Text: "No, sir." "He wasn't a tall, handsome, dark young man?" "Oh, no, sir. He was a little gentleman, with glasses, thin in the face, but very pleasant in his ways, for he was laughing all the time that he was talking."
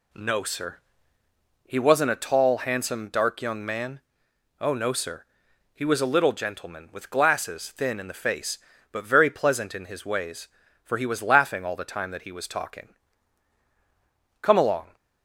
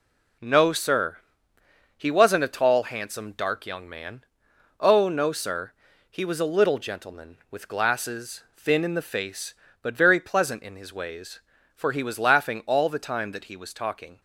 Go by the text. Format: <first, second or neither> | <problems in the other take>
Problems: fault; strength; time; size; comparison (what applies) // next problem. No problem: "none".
second | goes on to say "Come along"; from 14.4 s on; 0.54 s long